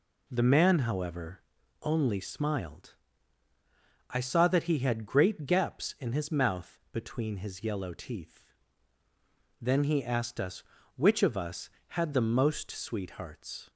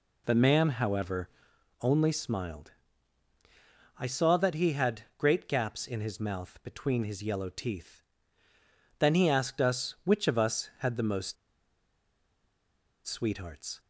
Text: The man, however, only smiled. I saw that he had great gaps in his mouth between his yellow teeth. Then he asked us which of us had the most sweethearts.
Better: first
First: none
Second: pauses between "had" and "great"; slight; at 5.0 s; 0.16 s long // pauses between "most" and "sweethearts"; strong; at 11.3 s; 1.7 s long

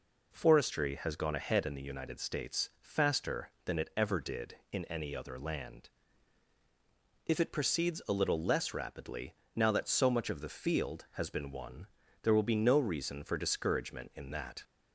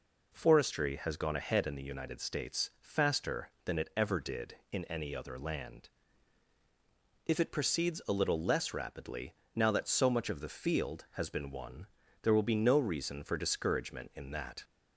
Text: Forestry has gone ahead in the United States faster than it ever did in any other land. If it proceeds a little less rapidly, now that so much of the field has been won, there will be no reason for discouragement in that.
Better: neither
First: none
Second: none

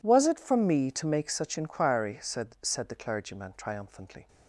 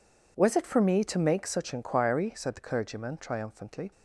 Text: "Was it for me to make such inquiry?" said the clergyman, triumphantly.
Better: second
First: says "said" twice; at 2.6 s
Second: none

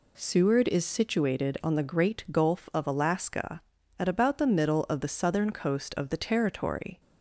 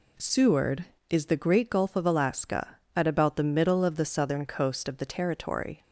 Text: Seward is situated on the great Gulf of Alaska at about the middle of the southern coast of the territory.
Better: first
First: none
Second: skips "situated on"; at 1.2 s

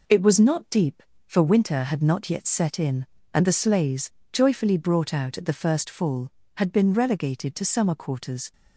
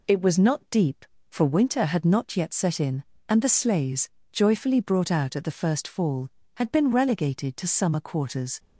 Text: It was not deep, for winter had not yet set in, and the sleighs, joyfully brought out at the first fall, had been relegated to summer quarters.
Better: second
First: gets quieter; noticeable; throughout; 4.5 dB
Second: none

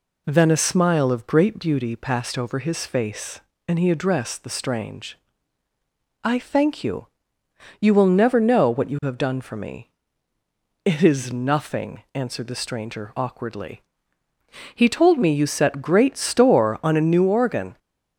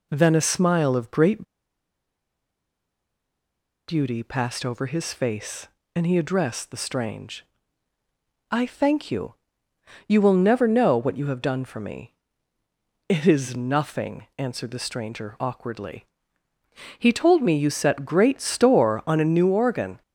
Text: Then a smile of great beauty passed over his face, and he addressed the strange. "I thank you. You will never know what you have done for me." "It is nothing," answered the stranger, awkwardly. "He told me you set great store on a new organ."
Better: first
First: none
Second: pauses between "great" and "beauty"; strong; at 1.4 s; 2.4 s long

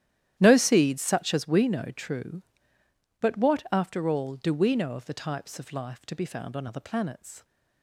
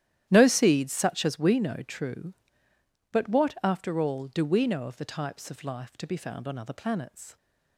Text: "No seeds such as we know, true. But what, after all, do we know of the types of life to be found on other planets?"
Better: neither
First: starts louder than the rest; strong; until 1.4 s; 11.5 dB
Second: starts louder than the rest; strong; until 1.3 s; 11.5 dB

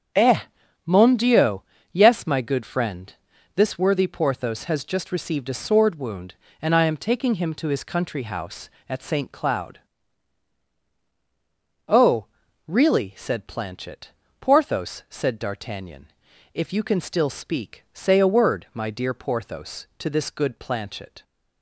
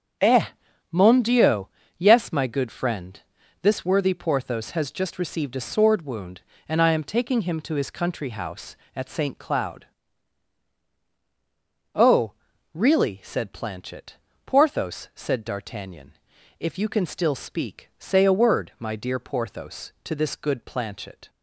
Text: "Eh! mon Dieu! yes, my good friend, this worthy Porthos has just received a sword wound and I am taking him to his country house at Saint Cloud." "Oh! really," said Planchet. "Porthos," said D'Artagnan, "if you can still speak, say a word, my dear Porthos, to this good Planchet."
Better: neither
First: starts louder than the rest; strong; until 1.5 s; 8 dB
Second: starts louder than the rest; strong; until 1.6 s; 8 dB

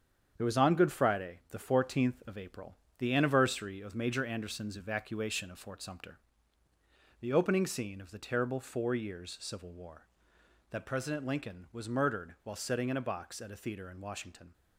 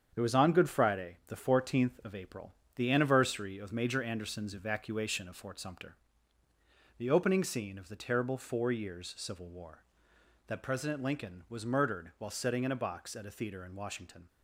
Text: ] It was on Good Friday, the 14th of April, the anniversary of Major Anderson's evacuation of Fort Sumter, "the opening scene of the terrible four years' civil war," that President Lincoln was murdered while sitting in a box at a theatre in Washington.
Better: neither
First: starts louder than the rest; strong; until 1.3 s; 7.5 dB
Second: starts louder than the rest; strong; until 1.1 s; 7.5 dB

